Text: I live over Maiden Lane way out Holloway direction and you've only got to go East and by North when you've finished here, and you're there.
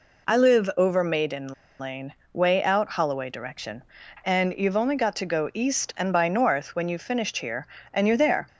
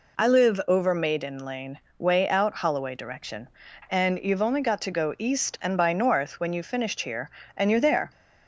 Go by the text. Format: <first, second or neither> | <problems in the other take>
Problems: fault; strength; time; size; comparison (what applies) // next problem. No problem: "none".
second | pauses between "Maiden" and "Lane"; slight; at 1.5 s; 0.28 s long // pauses between "Lane" and "way"; slight; at 2.1 s; 0.18 s long; slight in the second